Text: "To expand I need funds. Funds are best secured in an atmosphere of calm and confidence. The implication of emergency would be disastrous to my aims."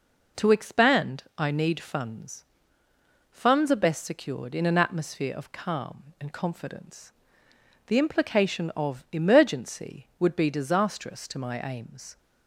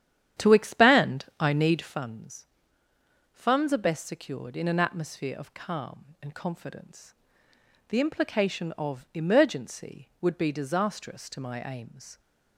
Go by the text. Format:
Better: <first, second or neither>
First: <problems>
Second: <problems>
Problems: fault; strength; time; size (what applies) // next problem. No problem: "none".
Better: first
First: none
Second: starts louder than the rest; strong; until 1.9 s; 10 dB